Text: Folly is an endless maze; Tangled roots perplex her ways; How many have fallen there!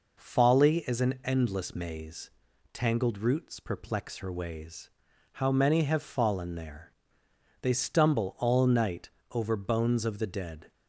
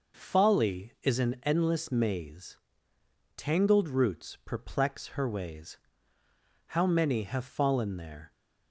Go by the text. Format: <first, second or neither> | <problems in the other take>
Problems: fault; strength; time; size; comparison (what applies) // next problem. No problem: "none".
second | goes on to say "They stumble all night over bones of the dead"; strong; from 7.6 s on; 3.1 s long